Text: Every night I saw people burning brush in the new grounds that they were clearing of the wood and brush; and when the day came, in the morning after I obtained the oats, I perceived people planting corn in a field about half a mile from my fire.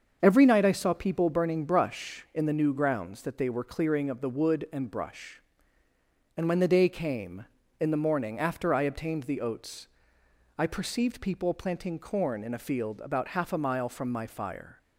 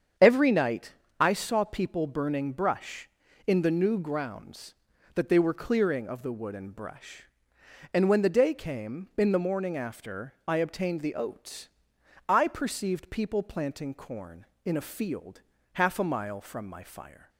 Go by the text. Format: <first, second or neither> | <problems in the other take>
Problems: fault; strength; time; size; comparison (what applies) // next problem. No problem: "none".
first | starts louder than the rest; strong; until 1.4 s; 8 dB; also in the first // pauses between "night" and "I"; slight; at 0.9 s; 0.28 s long // skips "about"; at 15.5 s